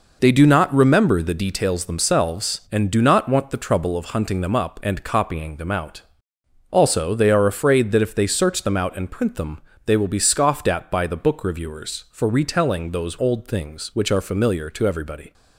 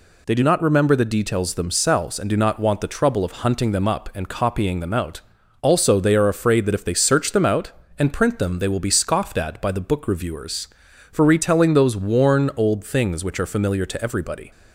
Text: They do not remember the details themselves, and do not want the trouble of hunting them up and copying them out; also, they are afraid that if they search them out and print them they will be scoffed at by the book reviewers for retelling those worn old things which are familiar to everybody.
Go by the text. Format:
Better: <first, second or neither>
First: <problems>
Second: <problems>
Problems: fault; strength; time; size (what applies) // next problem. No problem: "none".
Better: second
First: pauses between "them" and "they"; slight; at 9.6 s; 0.24 s long // skips "worn"; at 13.1 s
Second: none